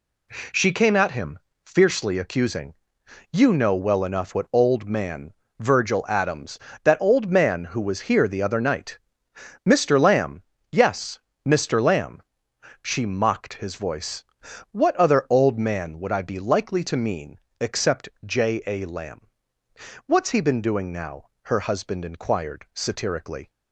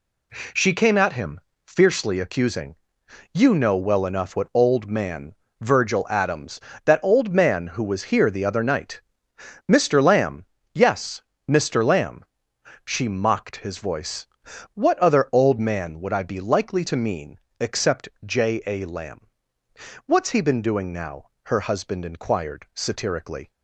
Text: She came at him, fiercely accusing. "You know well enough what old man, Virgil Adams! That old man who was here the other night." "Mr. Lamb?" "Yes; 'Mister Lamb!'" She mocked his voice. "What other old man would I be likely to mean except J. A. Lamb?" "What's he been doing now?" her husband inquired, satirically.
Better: neither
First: pauses between "mean" and "except"; slight; at 17.3 s; 0.22 s long // pauses between "except" and "J"; slight; at 18.0 s; 0.16 s long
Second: pauses between "mean" and "except"; slight; at 17.3 s; 0.22 s long // pauses between "except" and "J"; slight; at 18.0 s; 0.16 s long

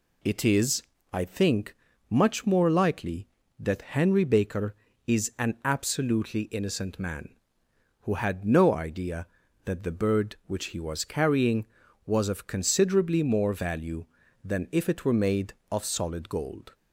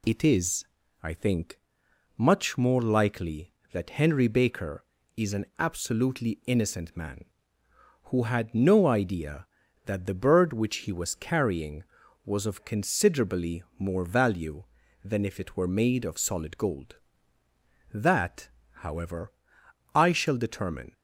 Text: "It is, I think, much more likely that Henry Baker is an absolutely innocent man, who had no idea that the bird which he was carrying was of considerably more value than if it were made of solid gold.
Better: first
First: none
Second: pauses between "considerably" and "more"; slight; at 13.6 s; 0.16 s long // goes on to say "That however I shall determine"; strong; from 17.9 s on; 3.0 s long

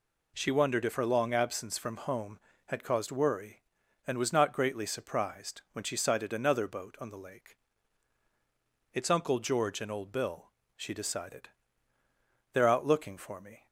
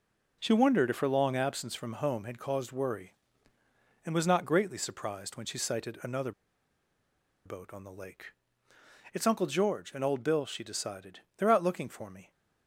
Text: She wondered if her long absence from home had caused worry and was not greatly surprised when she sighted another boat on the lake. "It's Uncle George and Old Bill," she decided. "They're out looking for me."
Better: first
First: none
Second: pauses between "another" and "boat"; at 6.3 s; 1.1 s long

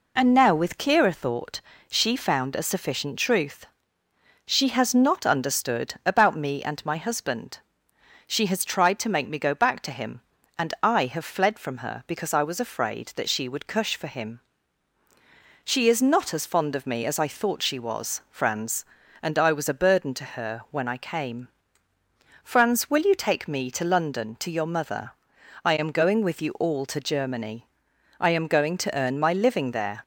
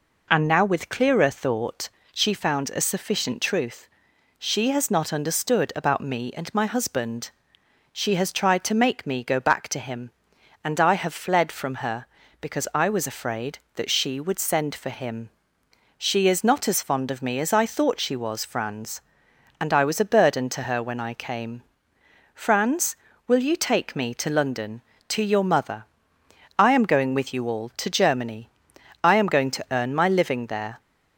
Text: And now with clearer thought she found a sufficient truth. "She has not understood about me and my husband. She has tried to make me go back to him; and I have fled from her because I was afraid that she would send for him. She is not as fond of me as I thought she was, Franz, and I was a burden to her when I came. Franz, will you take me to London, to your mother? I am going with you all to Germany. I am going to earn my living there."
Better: second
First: pauses between "thought" and "she"; slight; at 1.6 s; 0.30 s long // says "cush" for "send"; at 13.6 s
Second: pauses between "thought" and "she"; slight; at 1.8 s; 0.24 s long

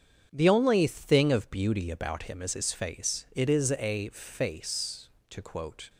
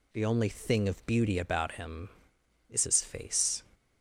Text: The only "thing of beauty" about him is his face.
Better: second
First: starts louder than the rest; strong; until 1.3 s; 8 dB // goes on to say "It is a face to quote"; strong; from 3.3 s on; 2.5 s long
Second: none

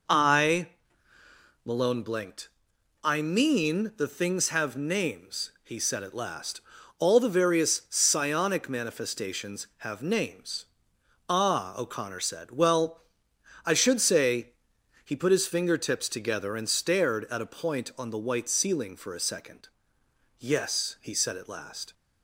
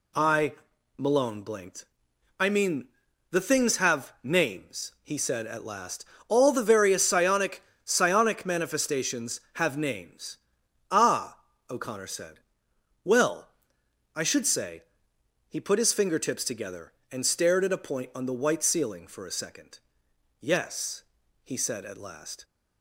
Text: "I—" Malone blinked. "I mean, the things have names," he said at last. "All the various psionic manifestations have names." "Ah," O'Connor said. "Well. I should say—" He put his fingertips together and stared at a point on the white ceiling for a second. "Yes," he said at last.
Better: first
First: none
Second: says "psionic" twice; at 7.8 s

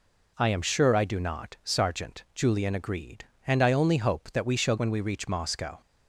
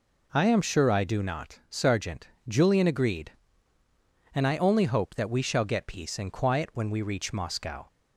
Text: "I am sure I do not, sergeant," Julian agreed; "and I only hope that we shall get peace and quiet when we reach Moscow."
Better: second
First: skips "get peace and quiet"; at 4.7 s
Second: none

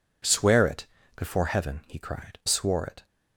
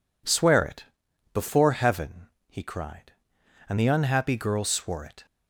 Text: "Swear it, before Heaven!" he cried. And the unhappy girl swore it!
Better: second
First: skips "And the unhappy girl"; at 2.4 s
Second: none

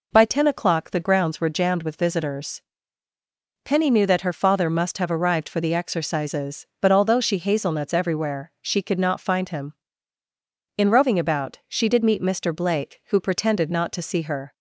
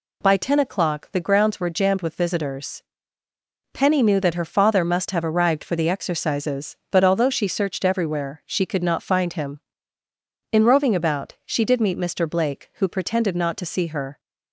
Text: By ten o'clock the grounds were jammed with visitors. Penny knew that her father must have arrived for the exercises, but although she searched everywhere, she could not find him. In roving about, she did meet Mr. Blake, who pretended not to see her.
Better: second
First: says "hazelnuts" for "searched"; at 7.3 s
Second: none

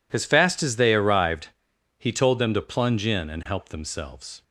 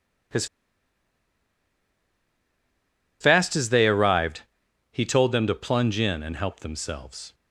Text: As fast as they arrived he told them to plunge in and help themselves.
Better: first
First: pauses between "arrived" and "he"; noticeable; at 1.4 s; 0.48 s long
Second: pauses between "As" and "fast"; strong; at 0.4 s; 2.7 s long // pauses between "arrived" and "he"; noticeable; at 4.4 s; 0.48 s long

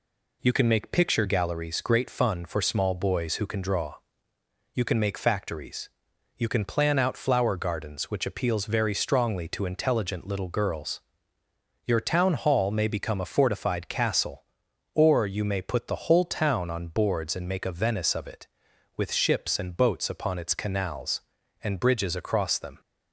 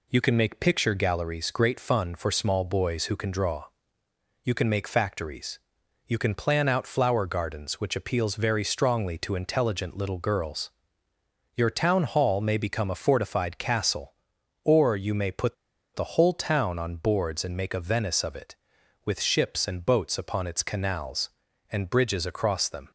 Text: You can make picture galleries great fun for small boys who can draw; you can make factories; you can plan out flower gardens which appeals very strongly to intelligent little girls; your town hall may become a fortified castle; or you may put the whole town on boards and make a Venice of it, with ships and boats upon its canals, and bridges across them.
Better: first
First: none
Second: pauses between "put" and "the"; at 15.5 s; 0.41 s long

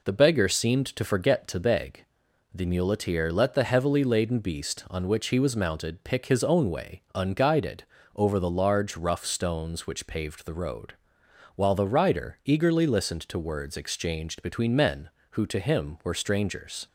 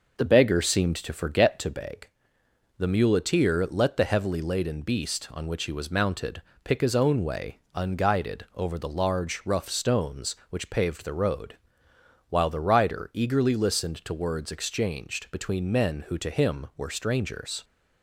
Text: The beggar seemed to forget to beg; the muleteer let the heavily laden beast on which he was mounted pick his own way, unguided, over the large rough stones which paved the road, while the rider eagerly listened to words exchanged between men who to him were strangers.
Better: first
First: none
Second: starts louder than the rest; noticeable; until 1.9 s; 5.5 dB // pauses between "mounted" and "pick"; slight; at 6.4 s; 0.22 s long

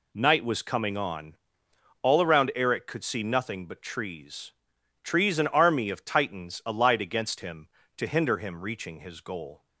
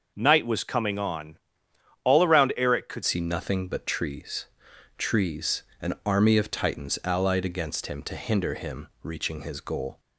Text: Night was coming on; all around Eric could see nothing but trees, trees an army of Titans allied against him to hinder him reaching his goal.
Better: first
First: none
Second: changes voice at "see"; from 3.0 s on; 6.9 s long // pauses between "trees" and "an"; slight; at 5.6 s; 0.20 s long // pauses between "him" and "reaching"; slight; at 8.8 s; 0.16 s long

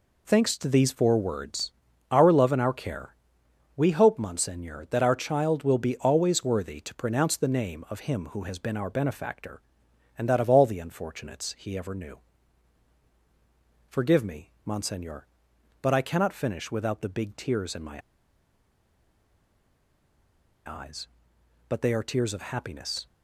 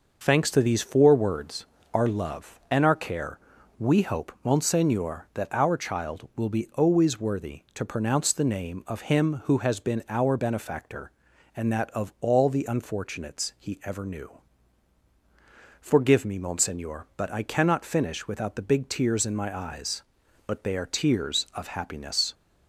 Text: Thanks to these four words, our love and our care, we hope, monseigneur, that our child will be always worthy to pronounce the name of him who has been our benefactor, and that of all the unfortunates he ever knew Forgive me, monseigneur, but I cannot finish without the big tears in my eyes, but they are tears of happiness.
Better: second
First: pauses between "knew" and "Forgive"; strong; at 12.1 s; 1.7 s long // pauses between "my" and "eyes"; strong; at 17.9 s; 2.6 s long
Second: pauses between "knew" and "Forgive"; strong; at 14.2 s; 1.5 s long

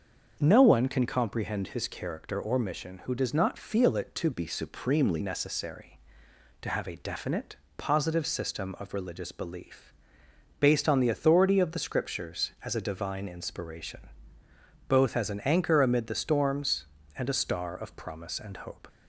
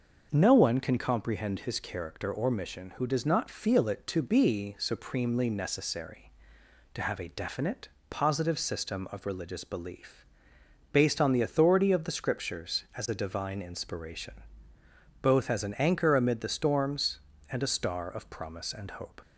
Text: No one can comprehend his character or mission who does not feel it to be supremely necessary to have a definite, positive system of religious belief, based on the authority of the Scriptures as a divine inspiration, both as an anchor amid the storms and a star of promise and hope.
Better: second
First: starts louder than the rest; until 1.4 s; 6.5 dB // changes voice from "be" to "supremely"; from 4.3 to 5.2 s; 0.9 s long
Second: starts louder than the rest; noticeable; until 1.3 s; 6 dB

